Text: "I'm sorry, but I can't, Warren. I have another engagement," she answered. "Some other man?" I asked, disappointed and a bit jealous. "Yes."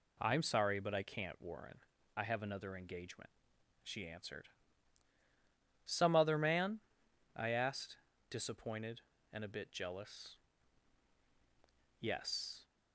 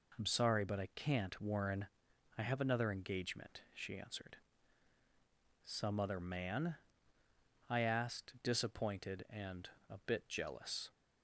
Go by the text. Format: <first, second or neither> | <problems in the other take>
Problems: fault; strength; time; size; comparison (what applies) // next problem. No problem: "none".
first | pauses between "and" and "a"; slight; at 9.7 s; 0.18 s long // stops before "Yes"; at 10.9 s